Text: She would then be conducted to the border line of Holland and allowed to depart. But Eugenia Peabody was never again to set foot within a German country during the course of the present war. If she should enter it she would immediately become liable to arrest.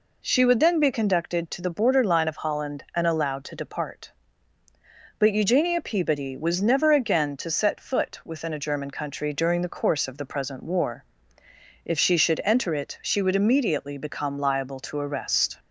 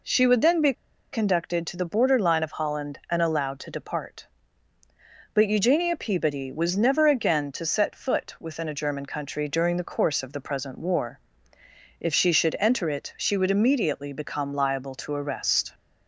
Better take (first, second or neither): first